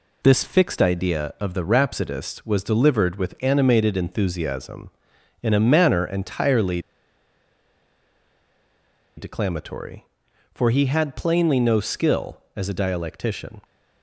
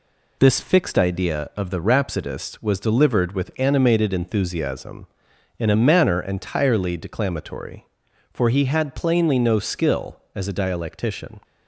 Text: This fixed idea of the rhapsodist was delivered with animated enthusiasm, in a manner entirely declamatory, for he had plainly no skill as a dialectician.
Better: second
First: pauses between "entirely" and "declamatory"; strong; at 6.7 s; 2.3 s long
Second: none

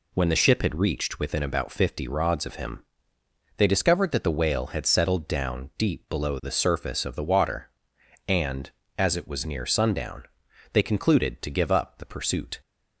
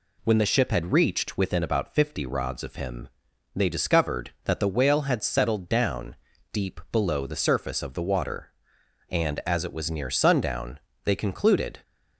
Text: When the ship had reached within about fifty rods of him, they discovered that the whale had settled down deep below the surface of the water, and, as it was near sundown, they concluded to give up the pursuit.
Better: first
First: none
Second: pauses between "down" and "deep"; slight; at 6.1 s; 0.36 s long // stops before "to give up the pursuit"; at 11.8 s

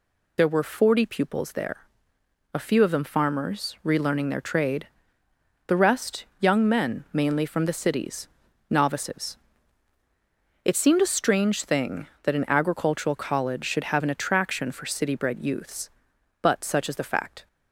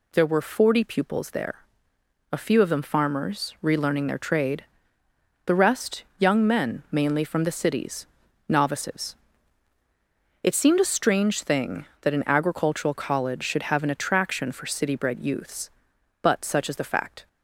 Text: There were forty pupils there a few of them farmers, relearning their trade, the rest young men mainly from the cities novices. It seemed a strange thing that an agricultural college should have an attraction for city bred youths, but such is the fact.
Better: second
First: loses the start of "There"; at 0.3 s; 40 ms // pauses between "there" and "a"; noticeable; at 1.8 s; 0.68 s long // pauses between "cities" and "novices"; at 8.2 s; 0.42 s long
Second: pauses between "there" and "a"; noticeable; at 1.6 s; 0.68 s long // pauses between "cities" and "novices"; at 8.0 s; 0.42 s long

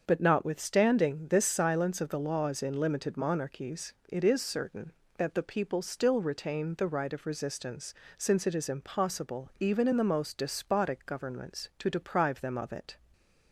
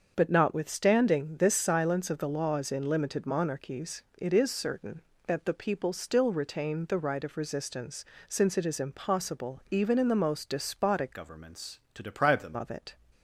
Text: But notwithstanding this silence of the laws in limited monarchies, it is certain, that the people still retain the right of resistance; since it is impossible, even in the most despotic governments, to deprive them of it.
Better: first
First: starts louder than the rest; until 1.0 s; 6.5 dB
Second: starts louder than the rest; until 1.1 s; 6.5 dB // changes voice from "governments" to "them"; from 11.1 to 12.5 s; 1.4 s long

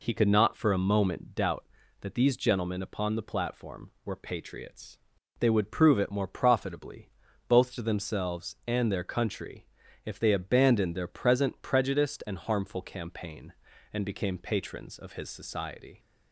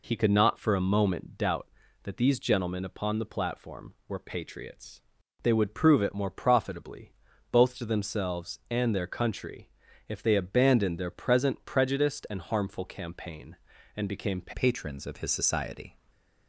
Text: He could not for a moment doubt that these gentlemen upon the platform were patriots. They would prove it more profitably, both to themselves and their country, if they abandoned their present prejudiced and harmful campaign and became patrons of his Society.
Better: first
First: none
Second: changes voice at "patrons"; from 14.5 s on; 1.4 s long // stays silent after the last word; slight; from 15.9 s on; 0.5 s long

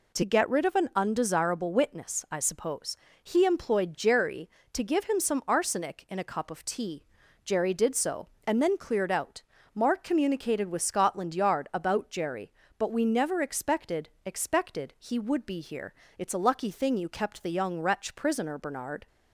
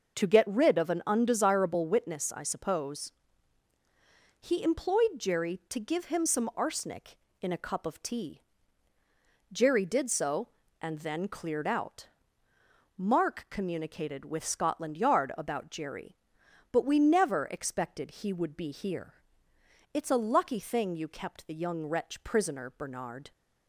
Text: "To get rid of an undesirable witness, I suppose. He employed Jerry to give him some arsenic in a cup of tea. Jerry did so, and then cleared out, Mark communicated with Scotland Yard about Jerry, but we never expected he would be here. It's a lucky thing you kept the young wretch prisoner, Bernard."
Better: second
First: says "expected" twice; at 14.2 s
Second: none

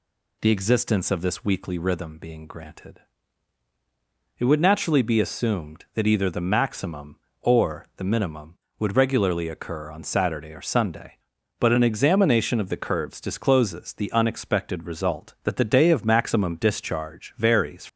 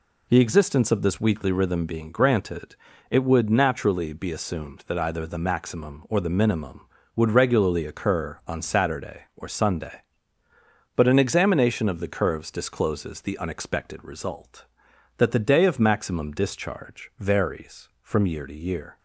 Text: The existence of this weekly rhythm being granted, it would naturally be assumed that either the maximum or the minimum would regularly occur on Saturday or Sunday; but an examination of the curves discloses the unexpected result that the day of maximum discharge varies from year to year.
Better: second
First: stops before "from year to year"; at 17.8 s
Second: none

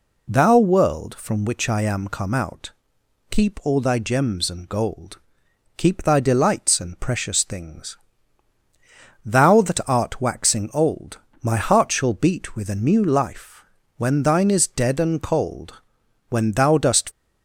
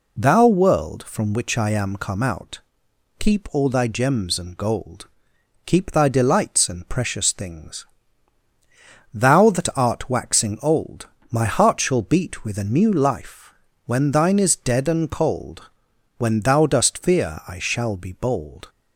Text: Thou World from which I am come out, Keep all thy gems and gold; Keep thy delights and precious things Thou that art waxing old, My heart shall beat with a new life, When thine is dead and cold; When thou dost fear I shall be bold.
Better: second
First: pauses between "things" and "Thou"; strong; at 7.9 s; 1.2 s long // stops before "fear I shall be bold"; at 17.1 s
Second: pauses between "things" and "Thou"; strong; at 7.8 s; 1.2 s long

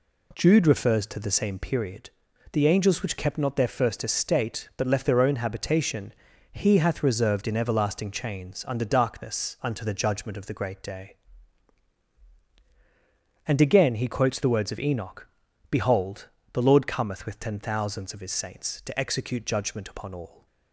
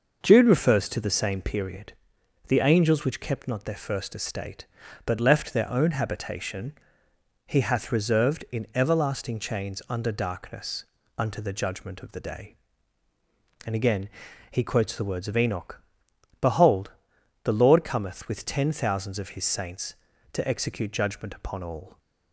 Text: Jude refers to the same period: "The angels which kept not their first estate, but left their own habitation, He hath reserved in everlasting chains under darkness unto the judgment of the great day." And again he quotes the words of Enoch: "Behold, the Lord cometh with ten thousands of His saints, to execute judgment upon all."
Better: first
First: none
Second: pauses between "darkness" and "unto"; slight; at 10.8 s; 0.34 s long // skips "great"; at 12.1 s // pauses between "again" and "he"; at 14.0 s; 0.44 s long

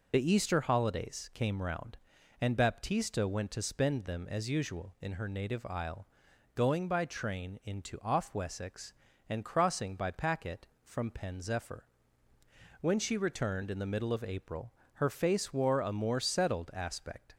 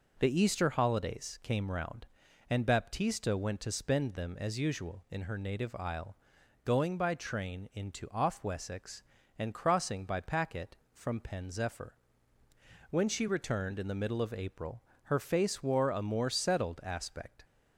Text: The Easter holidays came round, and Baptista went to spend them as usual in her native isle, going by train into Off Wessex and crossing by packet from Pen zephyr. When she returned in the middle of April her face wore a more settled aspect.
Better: second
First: loses the start of "The"; at 0.1 s; 60 ms // pauses between "April" and "her"; slight; at 14.7 s; 0.22 s long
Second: pauses between "April" and "her"; slight; at 14.8 s; 0.22 s long

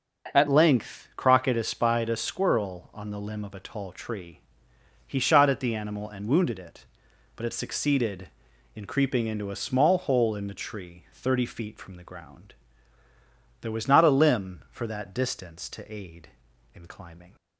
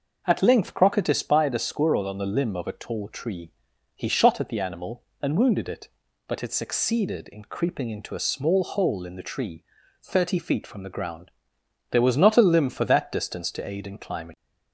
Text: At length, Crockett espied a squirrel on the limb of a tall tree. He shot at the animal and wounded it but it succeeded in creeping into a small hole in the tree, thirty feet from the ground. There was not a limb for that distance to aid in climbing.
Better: second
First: changes voice at "length"; from 0.4 s on; 16.9 s long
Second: none

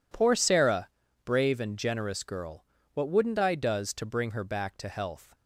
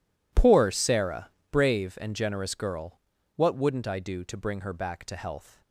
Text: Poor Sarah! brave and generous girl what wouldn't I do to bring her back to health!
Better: second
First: pauses between "girl" and "what"; slight; at 2.6 s; 0.30 s long // says "does" for "do"; at 3.5 s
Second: pauses between "girl" and "what"; at 2.9 s; 0.38 s long

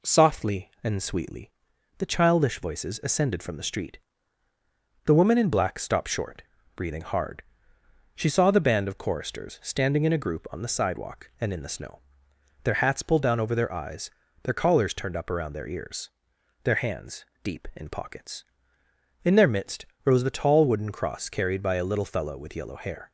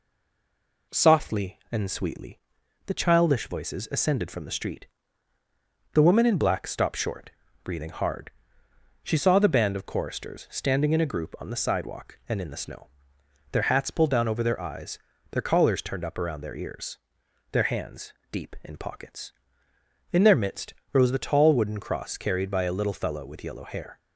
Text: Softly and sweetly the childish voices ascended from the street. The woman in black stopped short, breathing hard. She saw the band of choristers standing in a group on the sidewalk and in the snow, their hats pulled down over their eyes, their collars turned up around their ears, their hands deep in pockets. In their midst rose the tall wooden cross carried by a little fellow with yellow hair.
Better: first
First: pauses between "sweetly" and "the"; noticeable; at 1.5 s; 0.48 s long // pauses between "hands" and "deep"; slight; at 17.2 s; 0.16 s long // pauses between "midst" and "rose"; slight; at 19.8 s; 0.22 s long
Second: stays silent before the first word; slight; until 0.9 s; 0.9 s long // pauses between "sweetly" and "the"; noticeable; at 2.3 s; 0.48 s long // pauses between "hands" and "deep"; slight; at 18.1 s; 0.16 s long // pauses between "midst" and "rose"; slight; at 20.7 s; 0.22 s long

